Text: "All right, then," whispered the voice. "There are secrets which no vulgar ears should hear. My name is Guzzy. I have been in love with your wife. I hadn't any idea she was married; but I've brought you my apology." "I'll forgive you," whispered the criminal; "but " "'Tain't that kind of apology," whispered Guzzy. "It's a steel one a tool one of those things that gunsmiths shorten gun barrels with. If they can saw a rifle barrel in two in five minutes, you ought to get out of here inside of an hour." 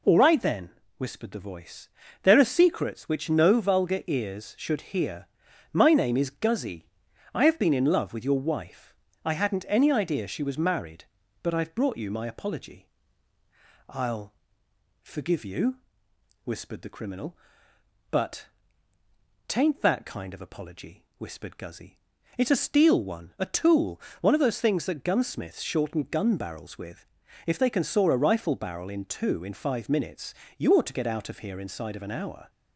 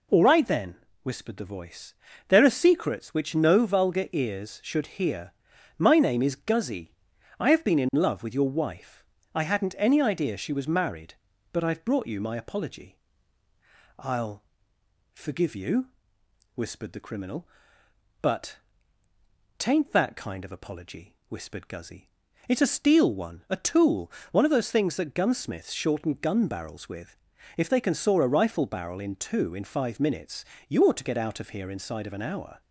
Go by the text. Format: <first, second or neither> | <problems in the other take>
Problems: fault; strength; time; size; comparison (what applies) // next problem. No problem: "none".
neither | pauses between "I'll" and "forgive"; noticeable; the same in both // pauses between "tool" and "one"; slight; the same in both